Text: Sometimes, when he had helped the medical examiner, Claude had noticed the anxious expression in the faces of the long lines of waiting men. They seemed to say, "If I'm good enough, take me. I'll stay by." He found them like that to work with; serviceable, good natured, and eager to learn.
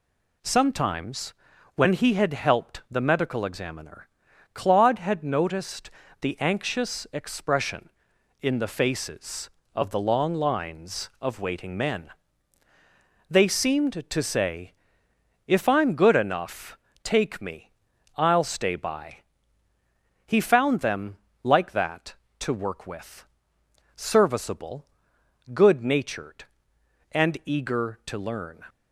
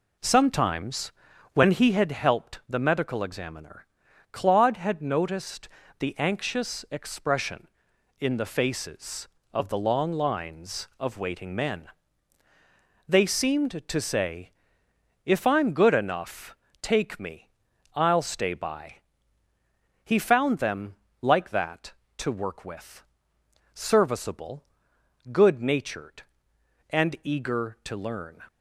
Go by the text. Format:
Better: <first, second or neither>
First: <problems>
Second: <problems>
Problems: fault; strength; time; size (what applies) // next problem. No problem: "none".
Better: first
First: pauses between "noticed" and "the"; slight; at 5.8 s; 0.32 s long // pauses between "them" and "like"; slight; at 21.1 s; 0.26 s long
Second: starts louder than the rest; until 2.1 s; 4 dB // pauses between "noticed" and "the"; slight; at 5.6 s; 0.32 s long // pauses between "them" and "like"; slight; at 20.9 s; 0.26 s long